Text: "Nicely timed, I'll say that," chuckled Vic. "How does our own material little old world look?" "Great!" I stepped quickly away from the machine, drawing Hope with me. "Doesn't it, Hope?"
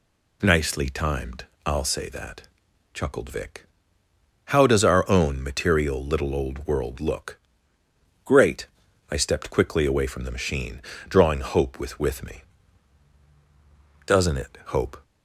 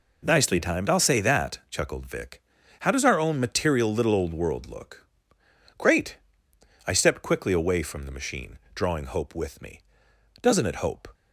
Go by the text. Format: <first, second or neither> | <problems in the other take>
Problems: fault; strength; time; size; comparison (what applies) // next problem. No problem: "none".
second | says "with" twice; at 11.9 s